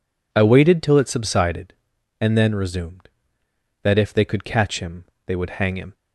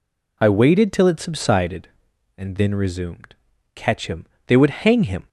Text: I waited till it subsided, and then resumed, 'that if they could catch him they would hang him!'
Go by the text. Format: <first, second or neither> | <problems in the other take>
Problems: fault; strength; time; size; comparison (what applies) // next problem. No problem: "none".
first | skips "that if they could"; at 3.5 s // pauses between "him" and "they"; slight; at 4.2 s; 0.22 s long; slight in the first